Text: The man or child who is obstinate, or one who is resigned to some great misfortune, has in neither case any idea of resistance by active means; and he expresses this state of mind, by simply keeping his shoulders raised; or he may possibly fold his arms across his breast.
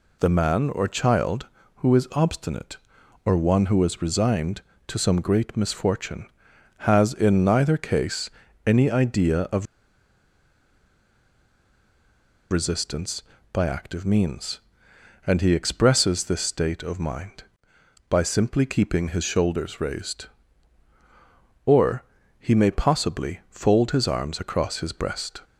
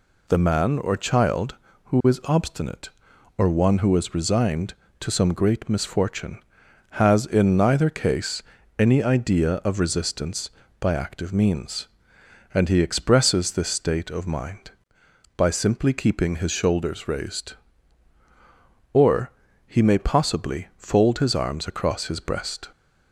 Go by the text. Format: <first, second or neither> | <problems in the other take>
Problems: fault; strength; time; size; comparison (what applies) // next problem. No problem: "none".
second | pauses between "case" and "any"; at 8.2 s; 0.38 s long; also in the second // pauses between "of" and "resistance"; strong; at 9.6 s; 2.8 s long // pauses between "or" and "he"; slight; at 22.0 s; 0.36 s long; slight in the second